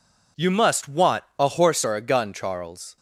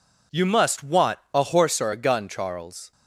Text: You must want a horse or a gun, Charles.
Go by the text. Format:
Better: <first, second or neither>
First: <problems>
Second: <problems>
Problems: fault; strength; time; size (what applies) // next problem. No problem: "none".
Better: neither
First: pauses between "want" and "a"; slight; at 1.2 s; 0.16 s long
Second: pauses between "want" and "a"; slight; at 1.1 s; 0.16 s long